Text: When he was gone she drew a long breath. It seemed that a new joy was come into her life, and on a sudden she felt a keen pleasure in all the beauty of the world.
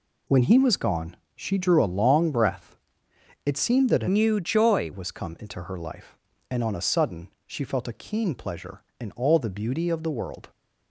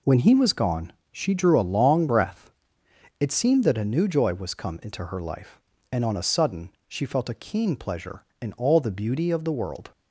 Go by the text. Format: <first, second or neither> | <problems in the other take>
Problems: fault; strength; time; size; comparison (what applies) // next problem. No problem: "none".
second | pauses between "gone" and "she"; slight; at 1.1 s; 0.20 s long; slight in the second // changes voice from "new" to "joy"; from 4.0 to 4.9 s; 0.9 s long // pauses between "sudden" and "she"; slight; at 7.2 s; 0.16 s long; slight in the second